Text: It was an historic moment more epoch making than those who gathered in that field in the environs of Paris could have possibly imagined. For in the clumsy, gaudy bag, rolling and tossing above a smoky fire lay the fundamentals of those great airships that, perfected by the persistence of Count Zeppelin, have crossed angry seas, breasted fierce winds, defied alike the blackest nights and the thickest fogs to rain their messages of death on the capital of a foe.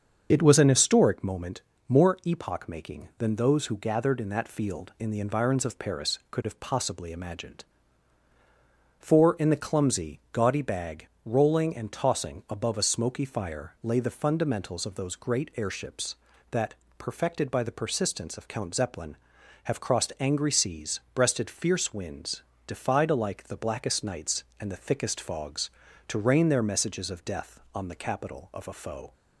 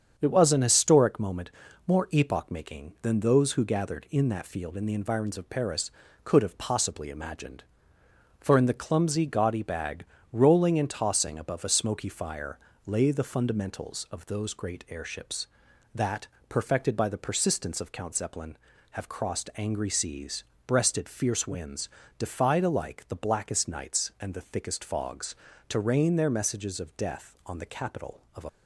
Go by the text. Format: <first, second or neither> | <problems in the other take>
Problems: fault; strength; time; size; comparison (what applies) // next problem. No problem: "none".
first | starts louder than the rest; strong; until 1.1 s; 7 dB; also in the first // pauses between "moment" and "more"; slight; at 1.5 s; 0.36 s long; slight in the first // pauses between "fire" and "lay"; slight; at 12.5 s; 0.28 s long // stops before "foe"; at 28.4 s